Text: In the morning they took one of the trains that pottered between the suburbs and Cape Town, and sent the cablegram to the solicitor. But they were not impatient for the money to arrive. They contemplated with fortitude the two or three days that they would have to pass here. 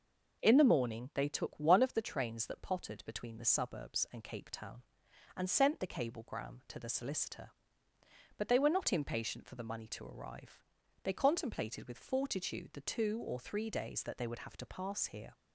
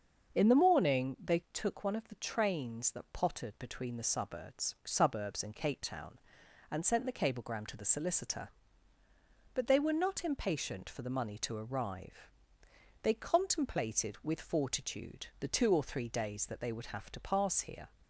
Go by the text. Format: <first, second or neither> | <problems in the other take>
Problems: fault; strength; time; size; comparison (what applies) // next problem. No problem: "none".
first | starts louder than the rest; until 1.4 s; 6.5 dB // says "suburbs" twice; at 4.8 s